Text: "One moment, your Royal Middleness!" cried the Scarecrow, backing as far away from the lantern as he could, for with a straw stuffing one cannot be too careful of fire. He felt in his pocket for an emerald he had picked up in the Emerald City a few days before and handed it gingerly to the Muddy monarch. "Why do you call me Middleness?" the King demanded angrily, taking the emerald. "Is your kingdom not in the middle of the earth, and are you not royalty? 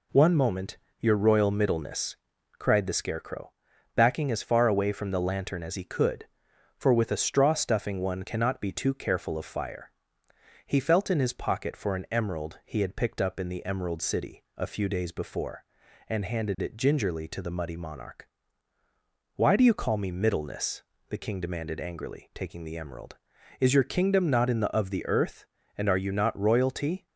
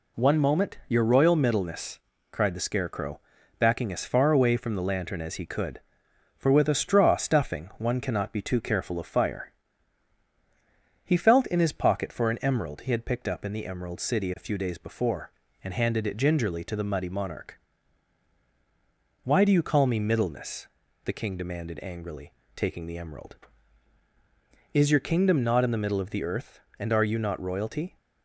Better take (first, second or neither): second